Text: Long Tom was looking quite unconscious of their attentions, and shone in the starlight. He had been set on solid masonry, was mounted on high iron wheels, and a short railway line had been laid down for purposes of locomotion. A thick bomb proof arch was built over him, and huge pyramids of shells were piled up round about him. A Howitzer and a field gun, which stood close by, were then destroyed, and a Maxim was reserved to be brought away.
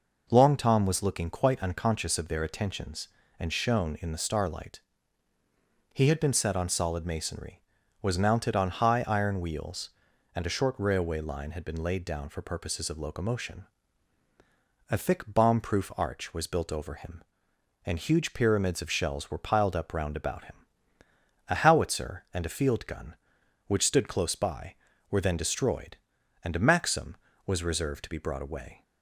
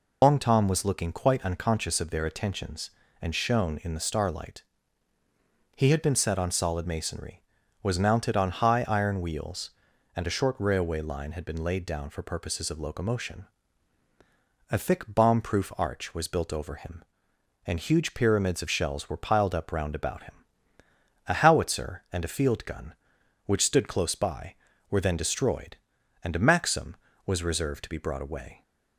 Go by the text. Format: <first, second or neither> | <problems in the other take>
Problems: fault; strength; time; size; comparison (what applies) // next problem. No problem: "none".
first | loses the start of "Long"; at 0.2 s; 110 ms